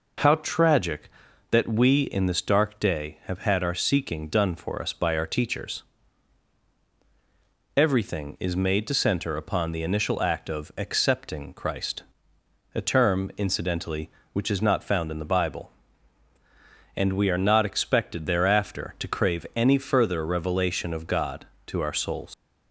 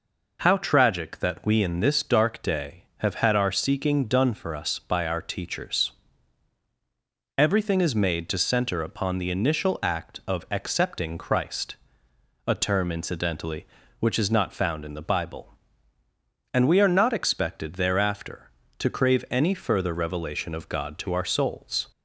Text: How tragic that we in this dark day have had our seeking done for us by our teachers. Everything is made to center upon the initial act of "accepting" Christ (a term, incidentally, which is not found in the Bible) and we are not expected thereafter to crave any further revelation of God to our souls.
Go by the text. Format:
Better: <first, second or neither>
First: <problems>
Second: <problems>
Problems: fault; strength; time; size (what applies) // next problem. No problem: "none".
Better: second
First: leaves "souls" unfinished; at 22.3 s; 140 ms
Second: none